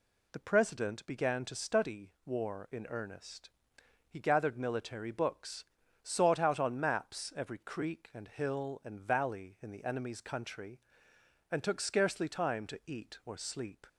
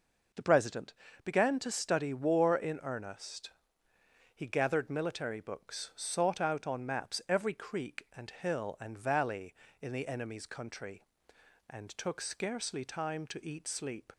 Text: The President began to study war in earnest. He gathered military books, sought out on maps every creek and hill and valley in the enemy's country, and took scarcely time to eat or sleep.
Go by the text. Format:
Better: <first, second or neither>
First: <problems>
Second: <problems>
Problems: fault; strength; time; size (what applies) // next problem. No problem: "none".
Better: first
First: none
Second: pauses between "President" and "began"; slight; at 0.9 s; 0.30 s long // skips "or"; at 13.6 s